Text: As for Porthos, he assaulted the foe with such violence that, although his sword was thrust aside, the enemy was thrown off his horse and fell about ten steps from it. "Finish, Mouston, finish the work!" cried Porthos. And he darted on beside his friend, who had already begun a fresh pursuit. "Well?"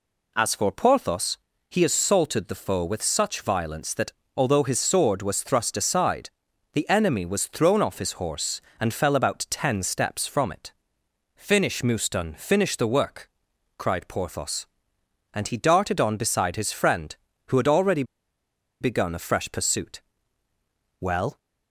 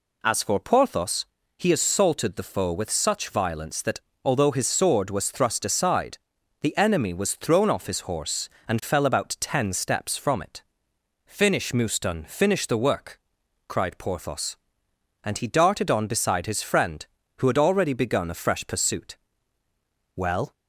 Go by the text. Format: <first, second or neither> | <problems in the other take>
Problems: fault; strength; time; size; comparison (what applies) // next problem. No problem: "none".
second | pauses between "already" and "begun"; noticeable; at 18.0 s; 0.77 s long